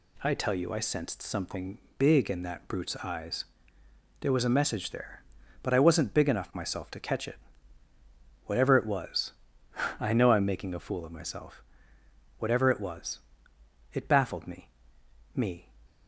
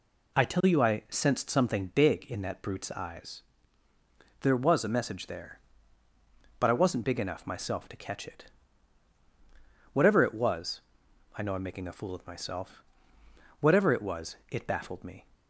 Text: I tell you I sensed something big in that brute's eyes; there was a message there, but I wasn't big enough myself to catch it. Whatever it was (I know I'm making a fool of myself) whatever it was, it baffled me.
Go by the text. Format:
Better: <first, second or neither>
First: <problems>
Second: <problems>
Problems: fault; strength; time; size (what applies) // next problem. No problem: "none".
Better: second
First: pauses between "something" and "big"; slight; at 1.7 s; 0.20 s long // says "me" twice; at 15.3 s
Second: none